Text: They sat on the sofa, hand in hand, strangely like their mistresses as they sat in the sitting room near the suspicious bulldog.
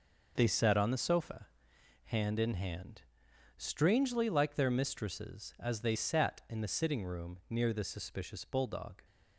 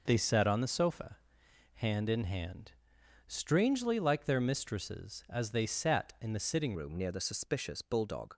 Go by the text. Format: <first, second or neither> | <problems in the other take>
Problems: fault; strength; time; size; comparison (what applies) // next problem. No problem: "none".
first | changes voice at "room"; from 6.7 s on; 1.6 s long